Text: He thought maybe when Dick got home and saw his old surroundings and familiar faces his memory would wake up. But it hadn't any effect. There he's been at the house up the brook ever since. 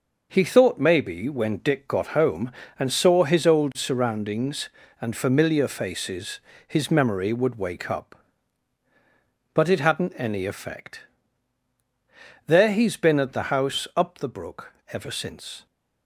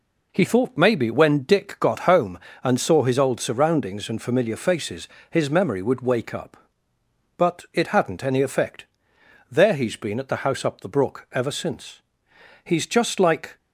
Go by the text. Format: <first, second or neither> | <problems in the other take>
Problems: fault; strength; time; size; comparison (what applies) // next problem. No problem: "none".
first | pauses between "faces" and "his"; slight; at 5.0 s; 0.22 s long; slight in the first // goes on to say "He's just like"; noticeable; from 12.6 s on; 0.92 s long